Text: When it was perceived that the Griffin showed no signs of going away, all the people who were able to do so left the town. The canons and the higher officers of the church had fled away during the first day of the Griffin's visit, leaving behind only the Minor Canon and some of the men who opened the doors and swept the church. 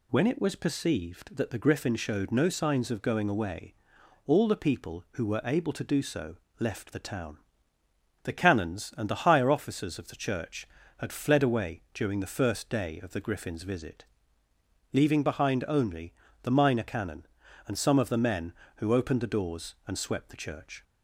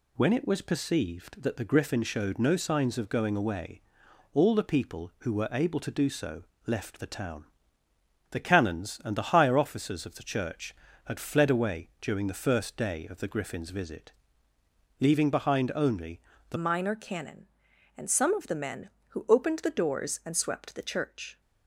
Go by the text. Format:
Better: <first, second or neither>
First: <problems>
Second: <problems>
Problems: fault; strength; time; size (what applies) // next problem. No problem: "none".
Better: first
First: pauses between "so" and "left"; slight; at 6.3 s; 0.24 s long // pauses between "only" and "the"; slight; at 16.1 s; 0.30 s long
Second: pauses between "so" and "left"; slight; at 6.4 s; 0.24 s long // pauses between "only" and "the"; slight; at 16.1 s; 0.30 s long // changes voice at "Minor"; from 16.5 s on; 4.9 s long